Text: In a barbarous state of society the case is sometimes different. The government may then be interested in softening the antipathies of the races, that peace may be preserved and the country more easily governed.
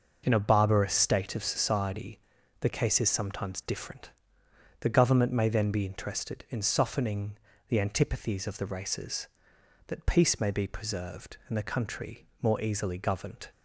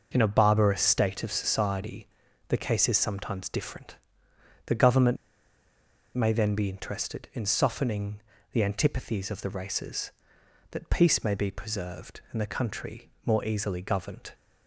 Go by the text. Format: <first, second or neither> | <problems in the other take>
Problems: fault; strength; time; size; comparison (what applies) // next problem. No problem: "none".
first | pauses between "society" and "the"; at 2.0 s; 0.42 s long; also in the first // pauses between "government" and "may"; at 5.1 s; 0.98 s long // pauses between "softening" and "the"; slight; at 8.2 s; 0.32 s long; slight in the first // pauses between "country" and "more"; slight; at 13.0 s; 0.16 s long; slight in the first